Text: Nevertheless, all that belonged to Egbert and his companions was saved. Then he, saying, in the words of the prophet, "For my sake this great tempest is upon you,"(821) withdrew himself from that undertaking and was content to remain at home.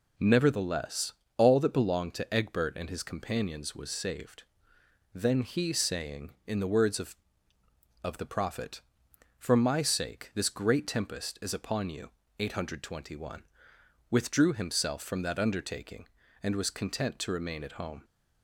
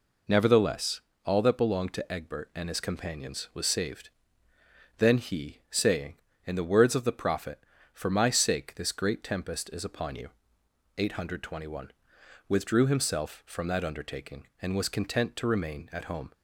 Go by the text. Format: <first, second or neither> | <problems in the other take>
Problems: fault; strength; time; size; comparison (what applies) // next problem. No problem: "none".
second | says "of" twice; at 8.0 s